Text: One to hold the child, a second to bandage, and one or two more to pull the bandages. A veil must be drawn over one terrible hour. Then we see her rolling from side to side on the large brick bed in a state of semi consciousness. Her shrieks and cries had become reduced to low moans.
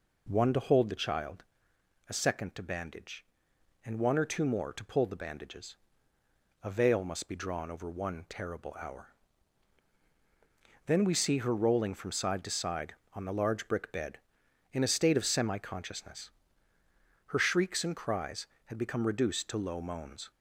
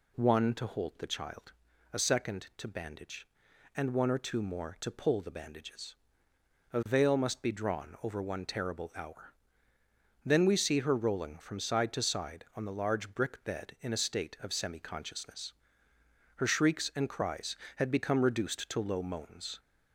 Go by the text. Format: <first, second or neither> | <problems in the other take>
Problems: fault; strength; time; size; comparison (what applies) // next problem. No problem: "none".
neither | none